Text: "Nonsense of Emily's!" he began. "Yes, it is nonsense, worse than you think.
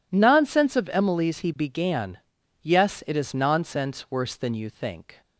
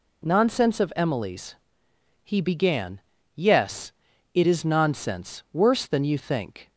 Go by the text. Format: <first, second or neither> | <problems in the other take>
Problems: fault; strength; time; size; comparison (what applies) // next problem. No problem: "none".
neither | none